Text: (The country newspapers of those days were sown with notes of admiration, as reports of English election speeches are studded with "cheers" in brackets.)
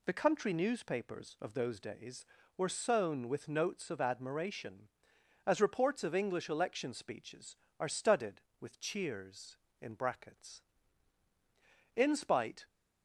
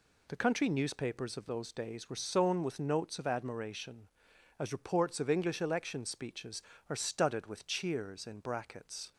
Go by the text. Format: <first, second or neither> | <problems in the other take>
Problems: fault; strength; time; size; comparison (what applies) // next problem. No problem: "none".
second | goes on to say "In spite"; noticeable; from 11.9 s on; 0.72 s long